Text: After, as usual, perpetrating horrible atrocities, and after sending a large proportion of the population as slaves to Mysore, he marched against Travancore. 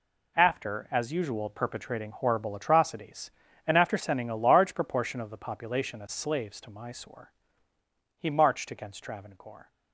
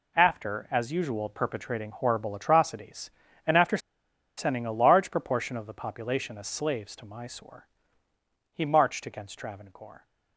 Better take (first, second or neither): first